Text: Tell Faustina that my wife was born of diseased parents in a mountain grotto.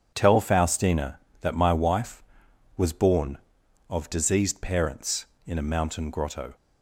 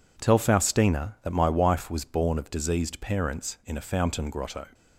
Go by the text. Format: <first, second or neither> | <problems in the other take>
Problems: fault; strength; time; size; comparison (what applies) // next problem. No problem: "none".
first | says "fountain" for "mountain"; at 3.8 s